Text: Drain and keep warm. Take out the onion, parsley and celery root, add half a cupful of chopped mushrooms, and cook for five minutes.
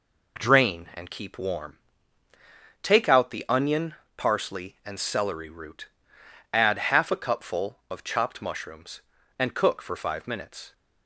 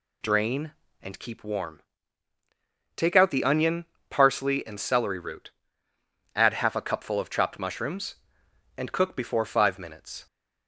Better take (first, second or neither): first